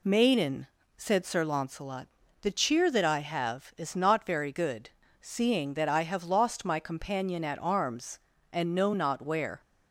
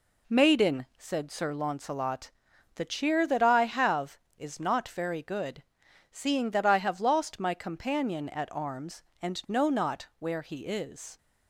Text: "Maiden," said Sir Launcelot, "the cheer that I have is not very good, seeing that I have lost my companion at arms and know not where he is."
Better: second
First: stops before "he is"; at 9.6 s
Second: none

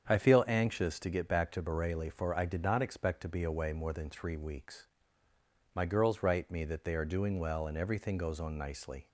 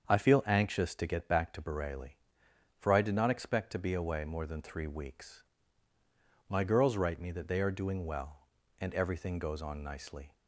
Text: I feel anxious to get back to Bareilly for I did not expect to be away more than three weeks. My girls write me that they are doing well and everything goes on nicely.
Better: neither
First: starts louder than the rest; strong; until 1.0 s; 8 dB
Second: starts louder than the rest; until 1.1 s; 7 dB

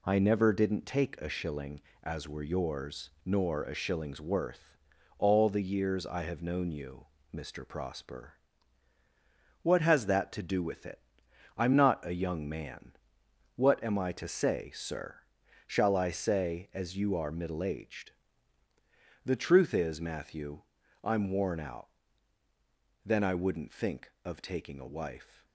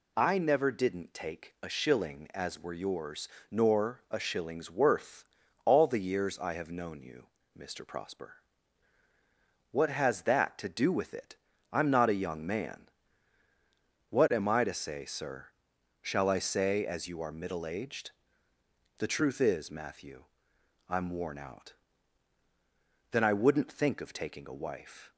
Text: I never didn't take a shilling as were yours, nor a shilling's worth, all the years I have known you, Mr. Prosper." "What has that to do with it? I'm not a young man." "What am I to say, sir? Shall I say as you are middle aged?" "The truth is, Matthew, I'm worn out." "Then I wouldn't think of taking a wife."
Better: second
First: gets quieter; noticeable; throughout; 4.5 dB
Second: none

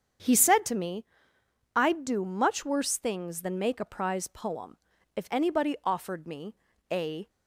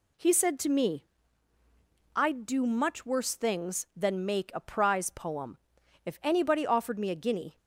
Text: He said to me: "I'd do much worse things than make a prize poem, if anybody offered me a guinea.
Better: second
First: starts louder than the rest; strong; until 1.9 s; 7.5 dB // pauses between "me" and "a"; slight; at 6.5 s; 0.36 s long // stops before "guinea"; at 7.2 s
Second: none

